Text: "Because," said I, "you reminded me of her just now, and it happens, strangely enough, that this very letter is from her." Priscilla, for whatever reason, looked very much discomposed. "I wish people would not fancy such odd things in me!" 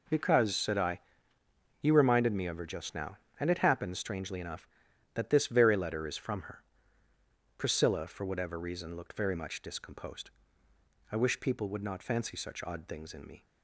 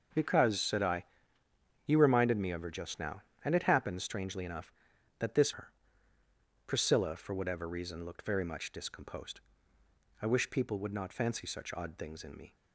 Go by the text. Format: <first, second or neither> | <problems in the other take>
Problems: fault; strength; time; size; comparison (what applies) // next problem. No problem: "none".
first | skips "very letter is from"; at 5.5 s